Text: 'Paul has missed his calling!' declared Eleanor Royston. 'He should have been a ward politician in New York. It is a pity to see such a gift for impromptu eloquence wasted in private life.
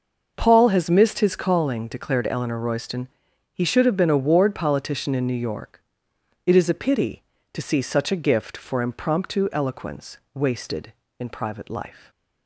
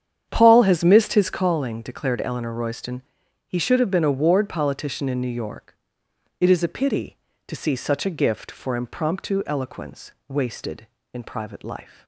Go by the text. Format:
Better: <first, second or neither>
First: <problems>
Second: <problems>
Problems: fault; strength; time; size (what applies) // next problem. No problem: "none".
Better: first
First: pauses between "eloquence" and "wasted"; slight; at 10.1 s; 0.16 s long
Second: starts louder than the rest; strong; until 1.4 s; 9 dB // pauses between "eloquence" and "wasted"; slight; at 10.1 s; 0.16 s long